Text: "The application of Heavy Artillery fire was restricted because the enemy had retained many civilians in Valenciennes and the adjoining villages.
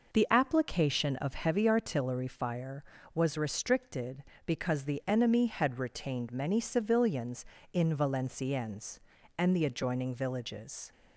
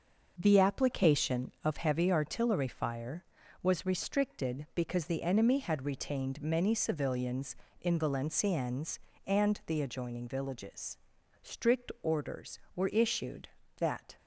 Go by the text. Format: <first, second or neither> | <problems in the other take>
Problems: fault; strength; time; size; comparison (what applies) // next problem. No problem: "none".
first | starts louder than the rest; noticeable; until 1.3 s; 6 dB // goes on to say "Strict orders were issued that"; strong; from 11.4 s on; 2.7 s long